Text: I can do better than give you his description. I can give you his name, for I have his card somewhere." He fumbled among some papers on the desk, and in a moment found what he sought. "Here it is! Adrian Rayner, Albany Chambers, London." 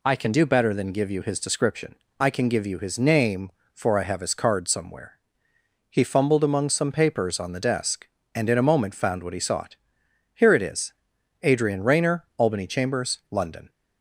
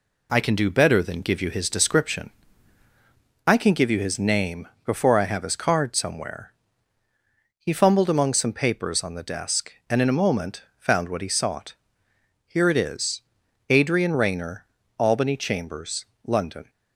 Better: first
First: none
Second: says "before" for "for"; at 4.8 s // pauses between "moment" and "found"; slight; at 10.6 s; 0.16 s long

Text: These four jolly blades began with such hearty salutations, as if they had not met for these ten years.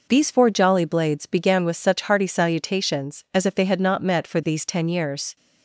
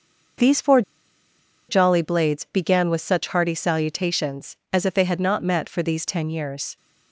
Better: first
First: none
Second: starts louder than the rest; until 2.2 s; 6.5 dB // pauses between "four" and "jolly"; noticeable; at 0.8 s; 0.87 s long

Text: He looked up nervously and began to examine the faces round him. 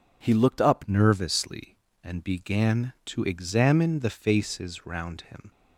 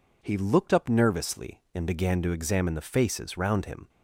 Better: second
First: changes voice at "nervously"; from 0.8 s on; 4.6 s long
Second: none

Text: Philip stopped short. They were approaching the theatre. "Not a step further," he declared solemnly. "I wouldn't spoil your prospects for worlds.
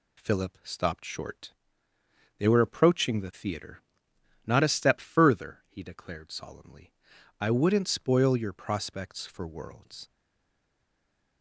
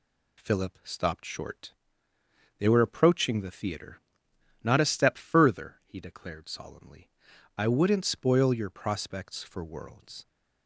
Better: second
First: stays silent after the last word; noticeable; from 10.1 s on; 1.3 s long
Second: none

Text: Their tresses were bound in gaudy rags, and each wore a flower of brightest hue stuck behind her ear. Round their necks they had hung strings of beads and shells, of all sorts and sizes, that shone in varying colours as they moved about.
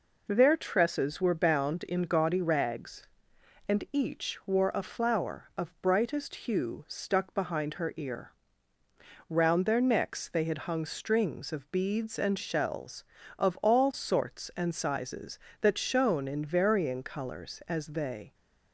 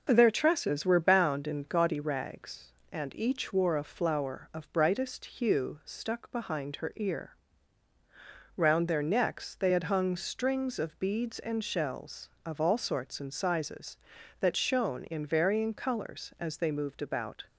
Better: second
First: stops before "moved about"; at 18.3 s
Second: none

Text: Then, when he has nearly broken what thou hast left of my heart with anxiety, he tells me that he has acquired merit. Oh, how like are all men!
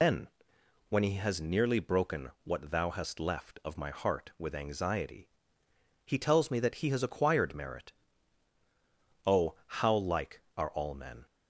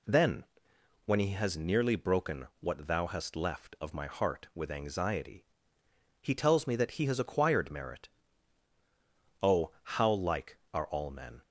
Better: second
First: loses the start of "Then"; at 0.0 s; 120 ms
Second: none

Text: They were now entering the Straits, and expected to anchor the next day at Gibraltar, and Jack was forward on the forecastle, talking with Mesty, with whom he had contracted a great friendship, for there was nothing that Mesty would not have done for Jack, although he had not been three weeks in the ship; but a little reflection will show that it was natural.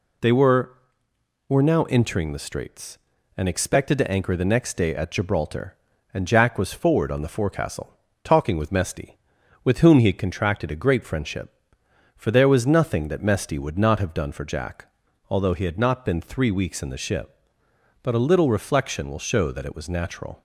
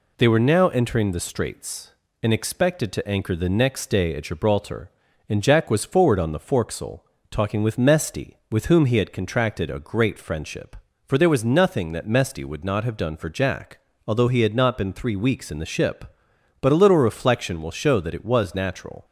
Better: second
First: says "were" twice; at 1.4 s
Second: none

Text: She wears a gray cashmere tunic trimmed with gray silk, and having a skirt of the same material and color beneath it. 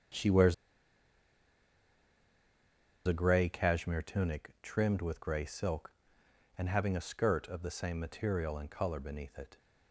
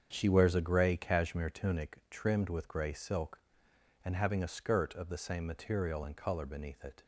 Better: second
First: starts louder than the rest; strong; until 3.6 s; 7.5 dB // pauses between "wears" and "a"; strong; at 0.5 s; 2.5 s long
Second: starts louder than the rest; strong; until 1.1 s; 7.5 dB

